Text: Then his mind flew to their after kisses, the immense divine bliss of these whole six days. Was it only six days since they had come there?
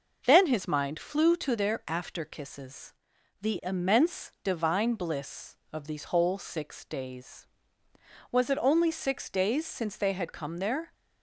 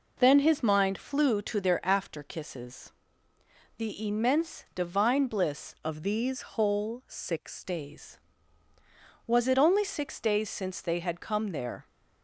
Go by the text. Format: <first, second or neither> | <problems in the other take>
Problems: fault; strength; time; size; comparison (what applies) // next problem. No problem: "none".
first | changes voice from "of" to "six"; from 5.8 to 7.6 s; 1.8 s long